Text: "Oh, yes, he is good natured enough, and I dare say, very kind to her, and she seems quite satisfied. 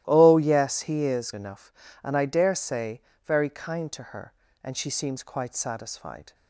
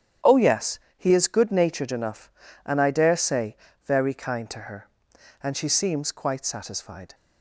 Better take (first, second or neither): second